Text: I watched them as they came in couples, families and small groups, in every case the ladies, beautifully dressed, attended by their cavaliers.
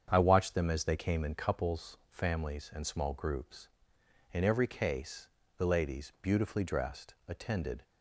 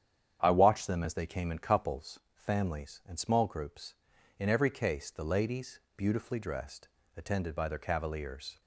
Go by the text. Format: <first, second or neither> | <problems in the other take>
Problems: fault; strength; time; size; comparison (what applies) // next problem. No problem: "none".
second | starts louder than the rest; strong; until 1.1 s; 7.5 dB; strong in the second // pauses between "case" and "the"; slight; at 5.2 s; 0.30 s long // stops before "by their cavaliers"; at 7.8 s